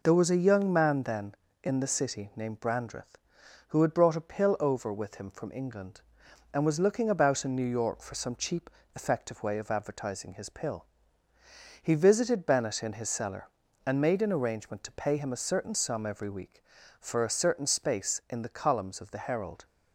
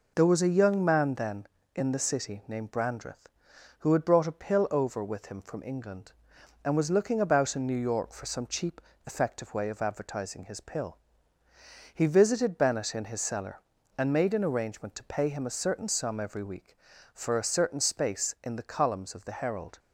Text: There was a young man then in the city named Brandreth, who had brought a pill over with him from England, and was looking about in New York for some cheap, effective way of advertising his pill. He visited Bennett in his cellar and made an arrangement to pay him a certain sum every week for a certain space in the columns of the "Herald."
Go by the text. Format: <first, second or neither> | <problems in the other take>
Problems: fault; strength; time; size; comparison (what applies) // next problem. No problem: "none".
neither | none